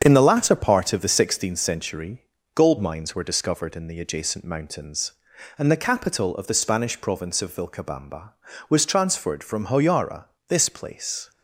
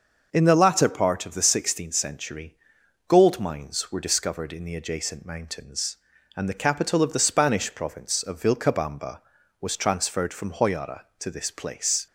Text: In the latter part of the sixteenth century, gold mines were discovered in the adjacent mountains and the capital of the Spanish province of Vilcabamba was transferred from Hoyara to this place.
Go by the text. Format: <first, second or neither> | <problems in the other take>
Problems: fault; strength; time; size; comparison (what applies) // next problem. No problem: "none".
second | starts louder than the rest; strong; until 1.0 s; 7 dB; also in the second // skips "to"; at 10.3 s